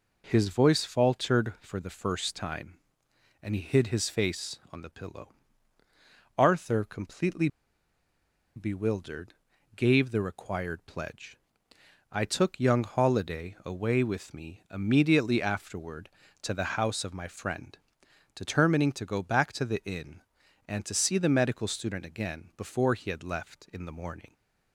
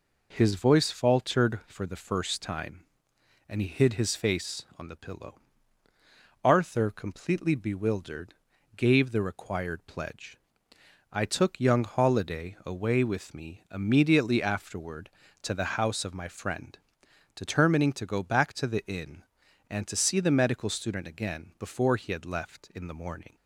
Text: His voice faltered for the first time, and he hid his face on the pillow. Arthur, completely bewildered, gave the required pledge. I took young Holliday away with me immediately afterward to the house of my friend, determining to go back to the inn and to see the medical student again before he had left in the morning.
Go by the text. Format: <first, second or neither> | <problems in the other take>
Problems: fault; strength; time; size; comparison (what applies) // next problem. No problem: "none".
second | pauses between "completely" and "bewildered"; at 7.4 s; 1.0 s long